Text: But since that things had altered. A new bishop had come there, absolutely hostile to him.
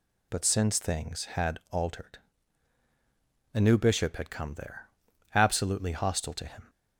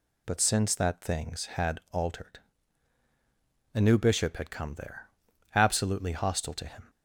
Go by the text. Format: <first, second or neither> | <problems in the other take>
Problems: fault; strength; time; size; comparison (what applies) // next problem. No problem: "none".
second | skips "that"; at 0.7 s